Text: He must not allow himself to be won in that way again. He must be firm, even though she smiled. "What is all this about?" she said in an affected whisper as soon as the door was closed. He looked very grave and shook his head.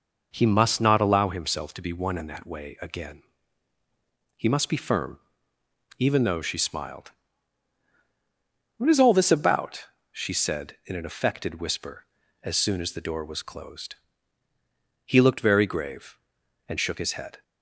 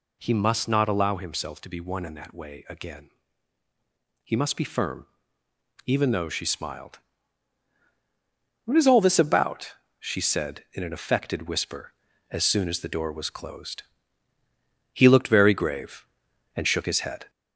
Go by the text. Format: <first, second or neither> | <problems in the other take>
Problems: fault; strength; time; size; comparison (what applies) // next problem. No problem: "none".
first | gets louder; slight; throughout; 2 dB